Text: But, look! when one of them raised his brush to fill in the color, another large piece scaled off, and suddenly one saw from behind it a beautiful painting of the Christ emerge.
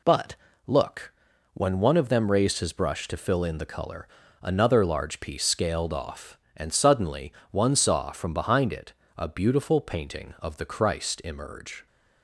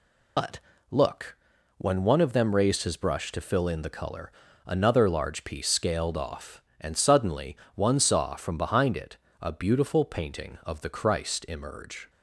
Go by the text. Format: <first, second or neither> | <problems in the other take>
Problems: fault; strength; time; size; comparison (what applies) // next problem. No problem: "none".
first | loses the start of "But"; at 0.3 s; 90 ms // pauses between "suddenly" and "one"; slight; at 7.5 s; 0.20 s long; slight in the first // pauses between "it" and "a"; slight; at 9.1 s; 0.24 s long; slight in the first